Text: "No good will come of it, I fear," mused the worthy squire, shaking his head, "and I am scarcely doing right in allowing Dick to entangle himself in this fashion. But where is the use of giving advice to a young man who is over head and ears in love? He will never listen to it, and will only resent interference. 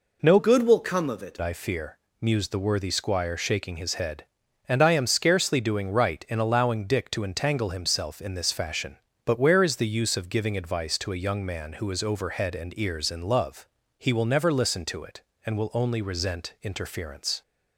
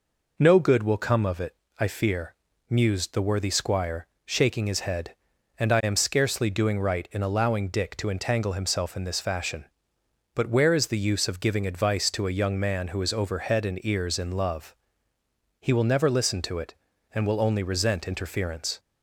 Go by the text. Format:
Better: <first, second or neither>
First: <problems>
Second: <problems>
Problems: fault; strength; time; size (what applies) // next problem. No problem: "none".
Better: second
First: changes voice from "good" to "it"; from 0.3 to 1.3 s; 1.0 s long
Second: none